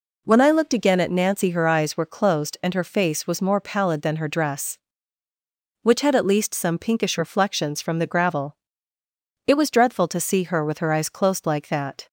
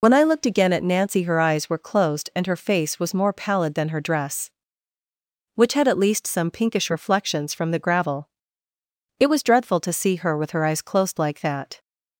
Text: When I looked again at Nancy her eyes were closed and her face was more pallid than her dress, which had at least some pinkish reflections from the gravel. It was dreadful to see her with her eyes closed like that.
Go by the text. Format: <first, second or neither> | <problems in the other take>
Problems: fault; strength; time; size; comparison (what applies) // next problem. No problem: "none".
first | loses the start of "When"; at 0.0 s; 50 ms